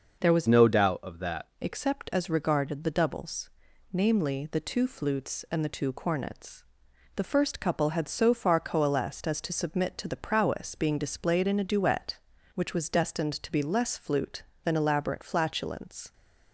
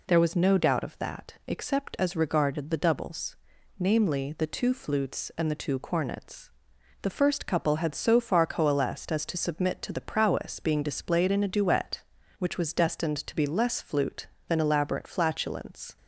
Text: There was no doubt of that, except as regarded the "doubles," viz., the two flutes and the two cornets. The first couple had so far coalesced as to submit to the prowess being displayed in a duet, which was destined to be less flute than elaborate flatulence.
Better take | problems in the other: second | changes voice from "no" to "that"; from 0.4 to 1.4 s; 1.0 s long

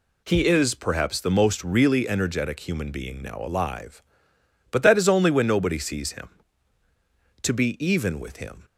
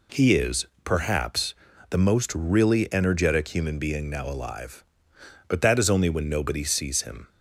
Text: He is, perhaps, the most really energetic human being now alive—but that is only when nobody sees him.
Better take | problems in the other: second | goes on to say "To be even with him"; noticeable; from 7.4 s on; 1.2 s long

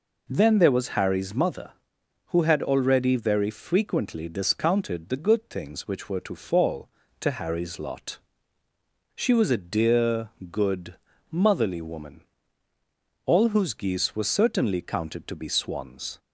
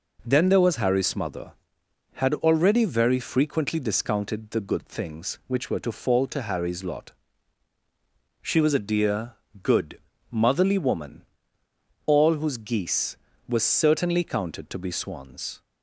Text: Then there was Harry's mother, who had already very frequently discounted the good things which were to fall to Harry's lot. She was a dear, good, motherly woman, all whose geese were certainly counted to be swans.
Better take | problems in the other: first | skips "who"; at 1.8 s

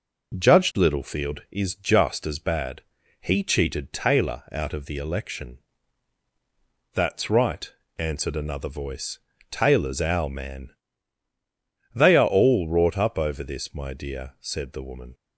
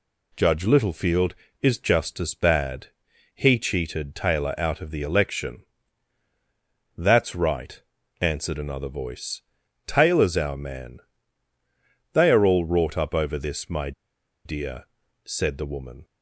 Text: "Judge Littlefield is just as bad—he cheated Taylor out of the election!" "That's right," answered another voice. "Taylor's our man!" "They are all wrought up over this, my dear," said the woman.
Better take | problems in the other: first | pauses between "my" and "dear"; noticeable; at 13.9 s; 0.54 s long

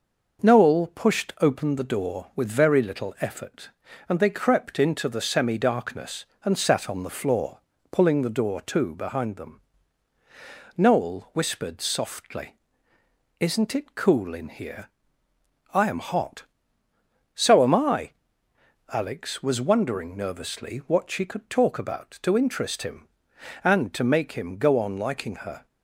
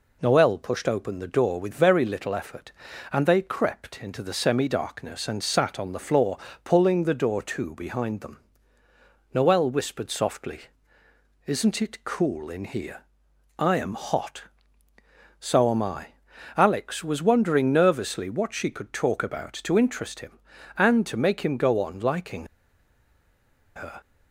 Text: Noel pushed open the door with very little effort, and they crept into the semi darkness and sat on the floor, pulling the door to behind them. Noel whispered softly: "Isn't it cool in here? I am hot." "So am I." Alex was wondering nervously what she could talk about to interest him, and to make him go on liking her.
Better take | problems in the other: first | pauses between "liking" and "her"; strong; at 22.4 s; 1.2 s long

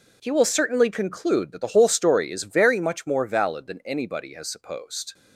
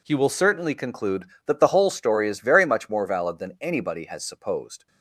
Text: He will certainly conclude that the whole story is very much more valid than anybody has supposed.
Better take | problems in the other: neither | none

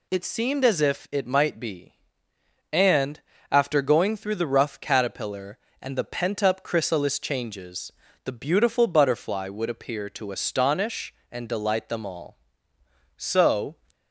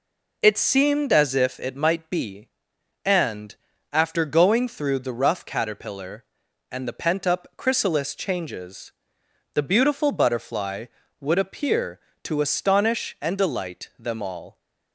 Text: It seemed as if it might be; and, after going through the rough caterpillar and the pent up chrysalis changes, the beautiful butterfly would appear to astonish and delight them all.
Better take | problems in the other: second | goes on to say "So"; noticeable; from 13.1 s on; 0.62 s long

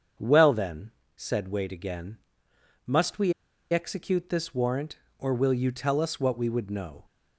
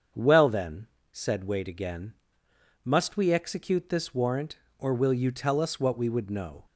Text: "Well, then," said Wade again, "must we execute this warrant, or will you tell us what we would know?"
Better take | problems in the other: second | starts louder than the rest; until 1.4 s; 7 dB; also in the second // pauses between "we" and "execute"; at 3.3 s; 0.40 s long

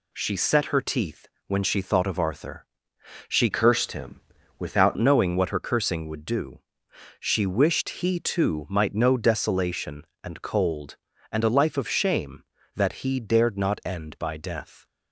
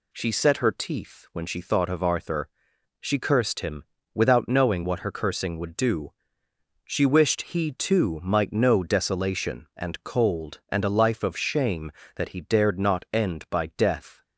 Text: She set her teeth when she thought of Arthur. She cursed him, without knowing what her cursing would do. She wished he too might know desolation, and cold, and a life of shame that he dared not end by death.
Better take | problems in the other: second | pauses between "teeth" and "when"; slight; at 1.2 s; 0.20 s long // changes voice from "cursed" to "without"; from 3.5 to 4.9 s; 1.4 s long

